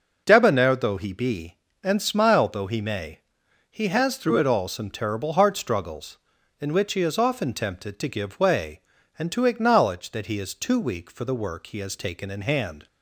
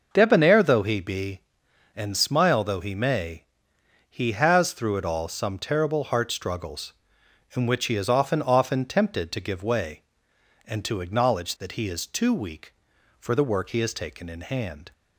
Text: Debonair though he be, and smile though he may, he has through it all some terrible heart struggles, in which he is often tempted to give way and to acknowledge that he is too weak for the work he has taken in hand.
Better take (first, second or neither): first